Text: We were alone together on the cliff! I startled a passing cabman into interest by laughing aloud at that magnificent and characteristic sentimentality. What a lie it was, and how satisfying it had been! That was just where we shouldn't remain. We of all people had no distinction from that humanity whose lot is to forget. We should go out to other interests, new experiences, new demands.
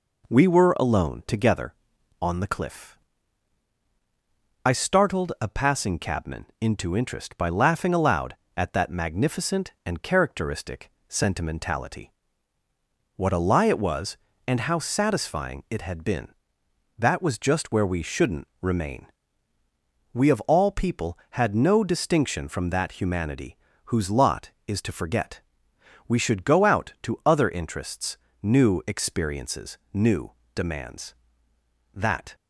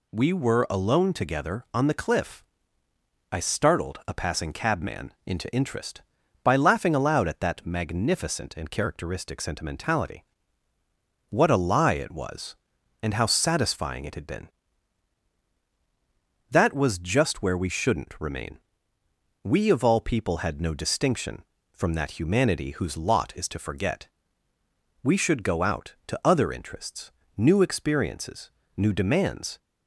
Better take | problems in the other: second | pauses between "characteristic" and "sentimentality"; slight; at 10.8 s; 0.20 s long // pauses between "shouldn't" and "remain"; slight; at 18.4 s; 0.16 s long // pauses between "humanity" and "whose"; slight; at 23.5 s; 0.28 s long // pauses between "new" and "demands"; slight; at 30.3 s; 0.22 s long // goes on to say "That"; slight; from 31.9 s on; 0.40 s long

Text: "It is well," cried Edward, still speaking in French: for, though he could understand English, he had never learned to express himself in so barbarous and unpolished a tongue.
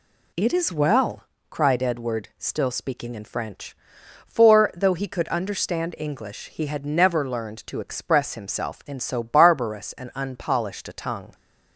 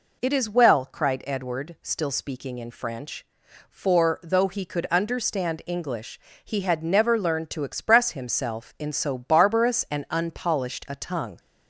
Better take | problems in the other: neither | none

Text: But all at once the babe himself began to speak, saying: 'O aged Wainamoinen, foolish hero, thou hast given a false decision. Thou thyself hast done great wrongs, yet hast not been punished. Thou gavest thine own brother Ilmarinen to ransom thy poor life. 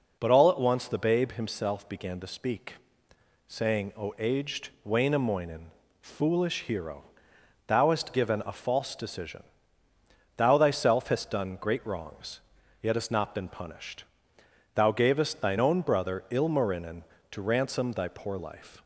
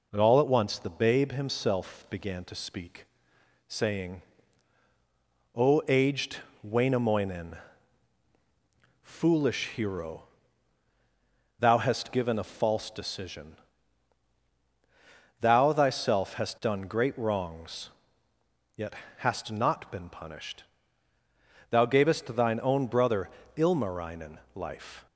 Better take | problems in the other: first | pauses between "aged" and "Wainamoinen"; slight; at 6.3 s; 0.26 s long // pauses between "yet" and "hast"; slight; at 18.9 s; 0.24 s long // pauses between "brother" and "Ilmarinen"; slight; at 23.3 s; 0.26 s long // skips "to ransom thy poor"; at 24.4 s

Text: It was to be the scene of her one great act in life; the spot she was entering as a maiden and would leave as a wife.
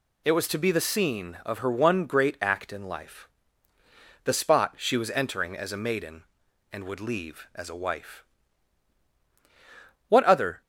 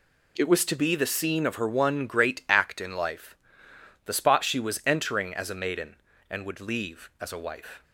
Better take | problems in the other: second | goes on to say "What other"; from 10.0 s on; 0.52 s long

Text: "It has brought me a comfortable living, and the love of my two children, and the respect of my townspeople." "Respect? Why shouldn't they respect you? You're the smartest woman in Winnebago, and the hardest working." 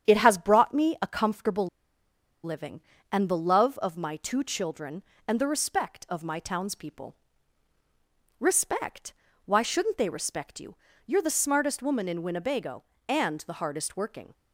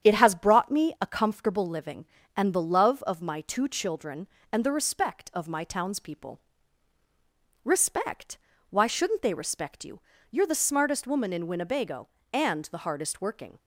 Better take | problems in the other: second | starts louder than the rest; strong; until 1.1 s; 9 dB; strong in the second // pauses between "comfortable" and "living"; noticeable; at 1.6 s; 0.77 s long

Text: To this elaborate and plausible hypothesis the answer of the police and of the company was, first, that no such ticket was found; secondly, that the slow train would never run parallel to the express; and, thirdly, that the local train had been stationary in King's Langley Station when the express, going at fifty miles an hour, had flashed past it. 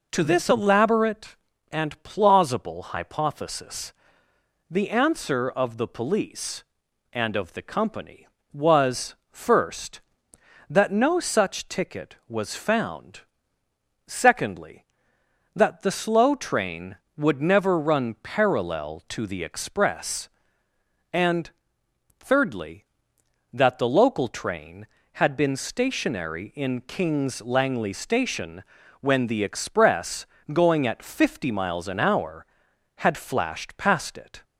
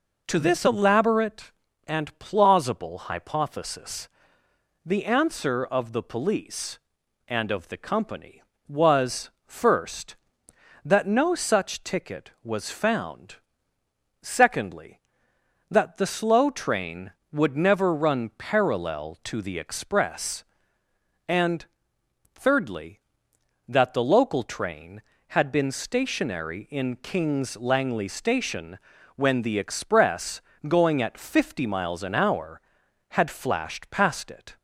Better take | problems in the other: neither | pauses between "hypothesis" and "the"; noticeable; the same in both // pauses between "Station" and "when"; the same in both

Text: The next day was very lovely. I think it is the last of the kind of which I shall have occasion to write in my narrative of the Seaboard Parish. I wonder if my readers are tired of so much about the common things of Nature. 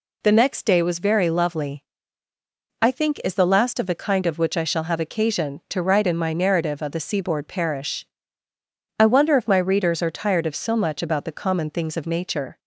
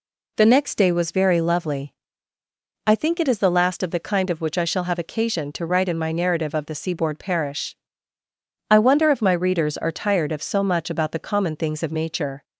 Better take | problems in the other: second | skips "it"; at 3.2 s

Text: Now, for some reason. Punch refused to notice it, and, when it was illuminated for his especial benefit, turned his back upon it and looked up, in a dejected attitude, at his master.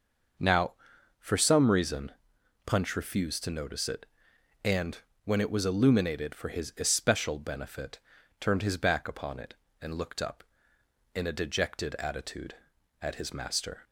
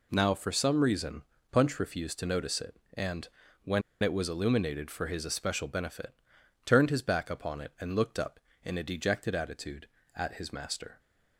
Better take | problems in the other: first | pauses between "when" and "it"; slight; at 3.8 s; 0.20 s long

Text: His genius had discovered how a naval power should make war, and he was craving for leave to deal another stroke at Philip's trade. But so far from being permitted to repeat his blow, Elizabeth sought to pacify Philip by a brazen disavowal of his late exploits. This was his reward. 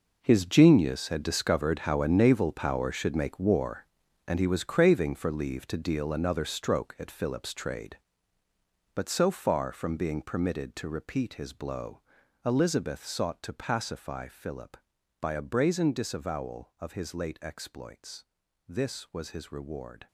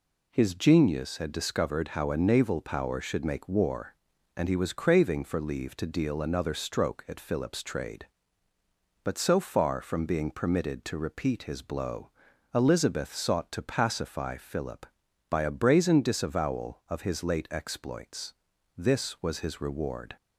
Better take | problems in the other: second | gets quieter; strong; throughout; 13 dB

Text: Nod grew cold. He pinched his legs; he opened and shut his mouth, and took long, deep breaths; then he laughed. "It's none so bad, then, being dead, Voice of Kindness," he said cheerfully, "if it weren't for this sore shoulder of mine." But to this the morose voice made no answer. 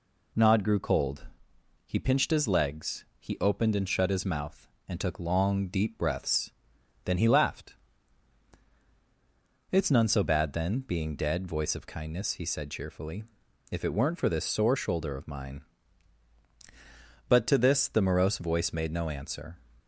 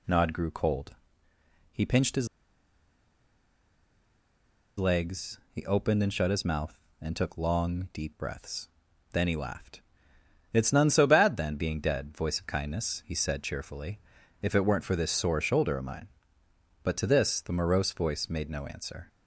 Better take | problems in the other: first | pauses between "his" and "legs"; strong; at 2.2 s; 2.5 s long

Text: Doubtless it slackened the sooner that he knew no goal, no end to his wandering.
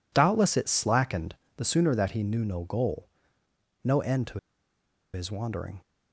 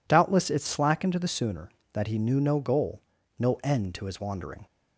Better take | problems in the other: second | pauses between "slackened" and "the"; slight; at 1.3 s; 0.20 s long // pauses between "to" and "his"; noticeable; at 4.3 s; 0.74 s long

